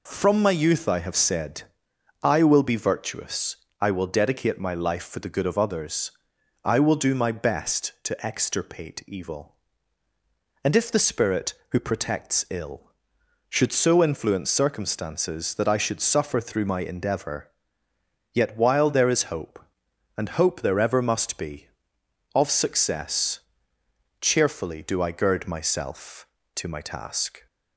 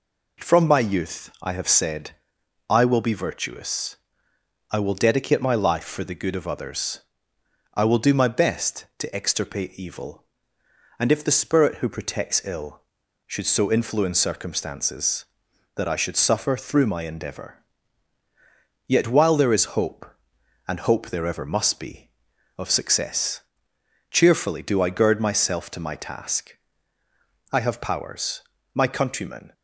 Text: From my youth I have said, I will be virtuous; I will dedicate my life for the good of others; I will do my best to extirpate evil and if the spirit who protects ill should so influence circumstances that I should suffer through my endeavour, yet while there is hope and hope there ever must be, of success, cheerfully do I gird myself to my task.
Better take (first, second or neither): first